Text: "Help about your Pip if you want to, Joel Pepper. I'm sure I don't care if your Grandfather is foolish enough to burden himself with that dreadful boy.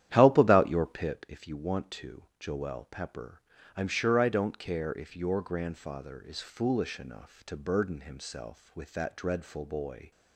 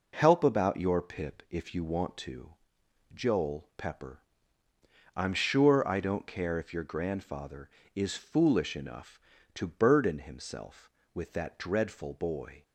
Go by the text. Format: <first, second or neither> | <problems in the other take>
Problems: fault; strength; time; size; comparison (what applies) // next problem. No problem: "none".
second | starts louder than the rest; strong; until 1.2 s; 11 dB